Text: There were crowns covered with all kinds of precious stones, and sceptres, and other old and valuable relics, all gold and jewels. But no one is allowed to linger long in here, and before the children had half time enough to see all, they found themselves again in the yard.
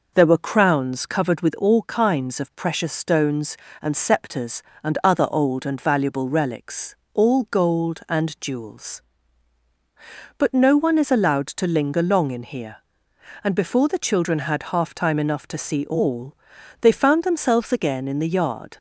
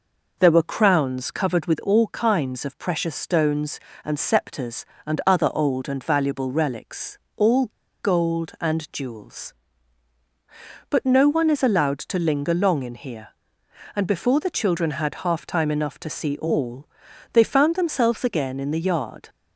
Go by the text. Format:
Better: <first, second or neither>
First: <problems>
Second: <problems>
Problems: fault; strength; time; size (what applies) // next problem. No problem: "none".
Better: first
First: none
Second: pauses between "all" and "gold"; at 7.6 s; 0.37 s long